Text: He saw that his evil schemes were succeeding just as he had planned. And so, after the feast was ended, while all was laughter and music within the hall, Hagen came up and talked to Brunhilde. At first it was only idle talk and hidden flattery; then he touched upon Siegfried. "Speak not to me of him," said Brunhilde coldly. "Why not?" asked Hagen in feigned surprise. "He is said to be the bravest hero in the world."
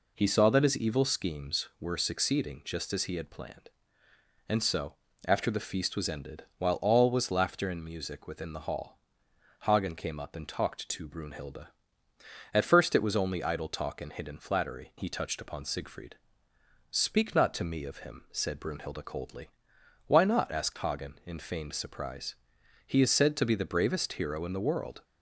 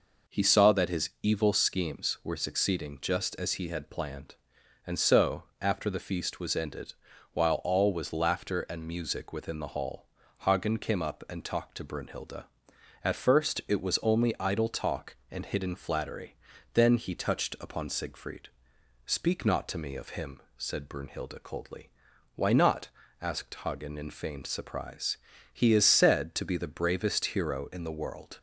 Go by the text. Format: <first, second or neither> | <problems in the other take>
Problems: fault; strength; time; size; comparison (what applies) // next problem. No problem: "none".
second | skips "then"; at 14.9 s